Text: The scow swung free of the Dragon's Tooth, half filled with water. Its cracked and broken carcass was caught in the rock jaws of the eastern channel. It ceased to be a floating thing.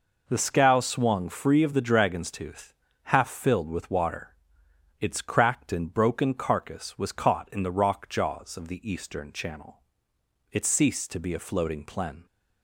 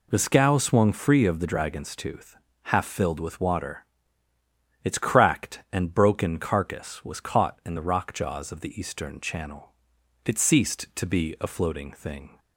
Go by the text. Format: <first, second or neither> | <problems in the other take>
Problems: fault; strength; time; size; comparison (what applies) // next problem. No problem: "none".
second | says "plen" for "thing"; at 11.8 s